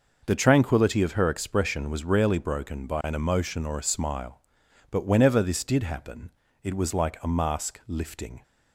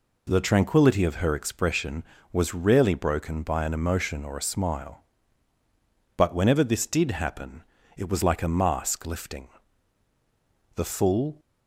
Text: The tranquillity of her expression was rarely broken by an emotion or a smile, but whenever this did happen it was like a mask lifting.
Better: first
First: pauses between "happen" and "it"; slight; at 6.3 s; 0.34 s long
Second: pauses between "happen" and "it"; slight; at 7.6 s; 0.32 s long // goes on to say "The full"; noticeable; from 10.7 s on; 0.64 s long

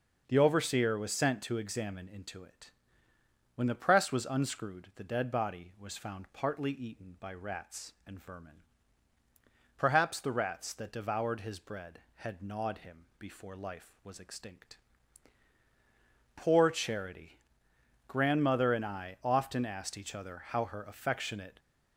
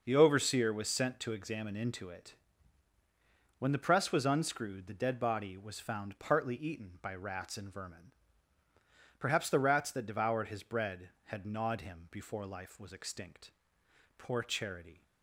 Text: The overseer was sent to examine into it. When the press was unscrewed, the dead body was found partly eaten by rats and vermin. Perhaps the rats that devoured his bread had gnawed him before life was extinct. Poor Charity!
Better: second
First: goes on to say "Grandmother and I often asked each other how her affectionate"; strong; from 18.0 s on; 3.5 s long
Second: none

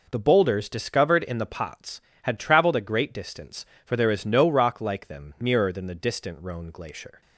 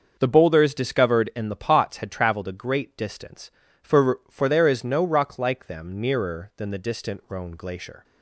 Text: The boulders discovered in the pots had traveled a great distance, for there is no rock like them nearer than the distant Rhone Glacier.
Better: first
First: none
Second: starts louder than the rest; until 1.2 s; 6.5 dB // says "for" twice; at 4.3 s

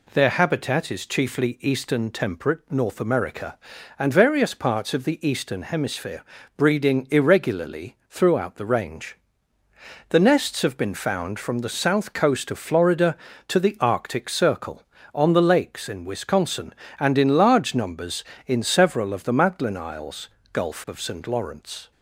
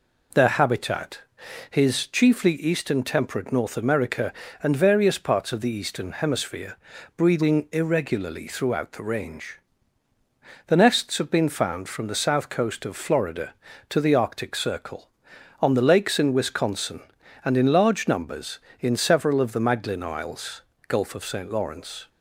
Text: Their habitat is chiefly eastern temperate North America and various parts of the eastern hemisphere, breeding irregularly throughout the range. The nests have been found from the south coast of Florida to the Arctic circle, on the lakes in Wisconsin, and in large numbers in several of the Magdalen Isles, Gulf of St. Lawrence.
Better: first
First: none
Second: says "his" for "is"; at 1.6 s

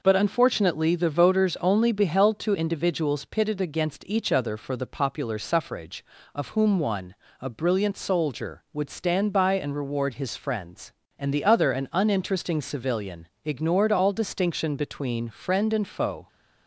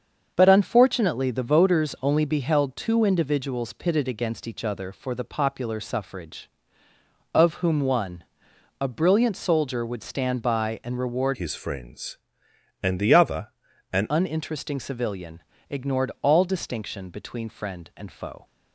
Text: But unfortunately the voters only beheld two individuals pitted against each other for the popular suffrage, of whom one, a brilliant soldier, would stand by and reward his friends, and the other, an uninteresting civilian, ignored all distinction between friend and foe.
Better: first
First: none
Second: starts louder than the rest; until 1.3 s; 7 dB // changes voice from "his" to "an"; from 11.3 to 14.0 s; 2.7 s long

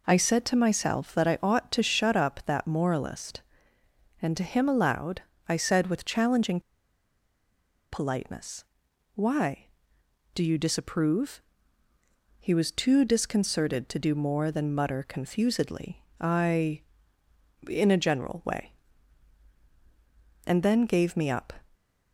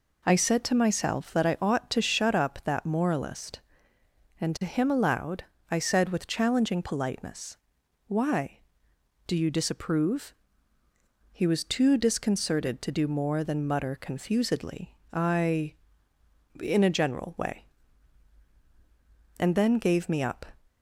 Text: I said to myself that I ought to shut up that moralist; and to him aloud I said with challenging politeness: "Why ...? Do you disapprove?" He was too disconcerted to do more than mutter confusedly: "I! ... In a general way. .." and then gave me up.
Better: second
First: pauses between "aloud" and "I"; slight; at 5.2 s; 0.26 s long // pauses between "challenging" and "politeness"; strong; at 6.5 s; 1.3 s long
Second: pauses between "aloud" and "I"; slight; at 5.4 s; 0.26 s long

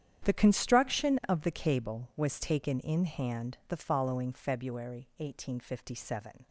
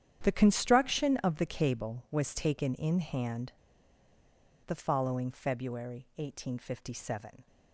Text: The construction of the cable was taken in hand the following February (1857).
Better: first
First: starts louder than the rest; strong; until 1.3 s; 9.5 dB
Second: starts louder than the rest; strong; until 1.2 s; 9.5 dB // pauses between "hand" and "the"; at 3.5 s; 1.1 s long

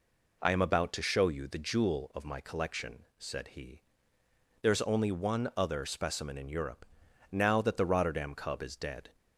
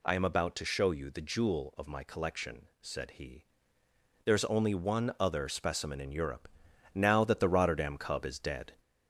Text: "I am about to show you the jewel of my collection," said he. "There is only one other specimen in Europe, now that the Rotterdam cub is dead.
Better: first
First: none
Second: gets louder; slight; throughout; 2.5 dB

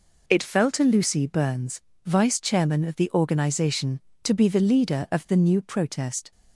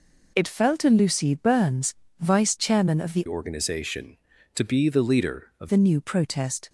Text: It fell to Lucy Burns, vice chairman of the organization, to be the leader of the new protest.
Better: first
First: none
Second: changes voice from "organization" to "of"; from 3.2 to 5.6 s; 2.4 s long

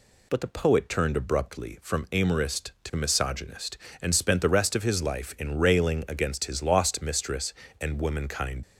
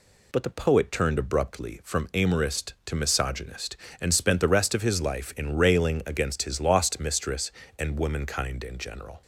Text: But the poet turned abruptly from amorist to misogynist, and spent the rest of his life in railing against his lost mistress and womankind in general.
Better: second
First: stops before "in general"; at 8.6 s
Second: none

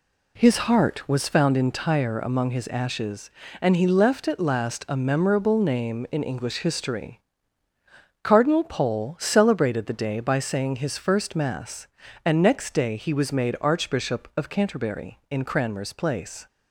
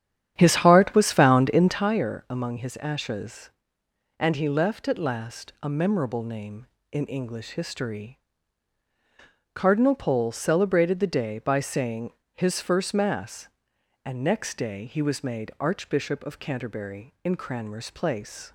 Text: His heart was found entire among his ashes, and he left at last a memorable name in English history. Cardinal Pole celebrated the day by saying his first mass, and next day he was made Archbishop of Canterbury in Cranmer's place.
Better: first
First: none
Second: starts louder than the rest; strong; until 1.9 s; 9.5 dB // pauses between "saying" and "his"; slight; at 12.1 s; 0.24 s long

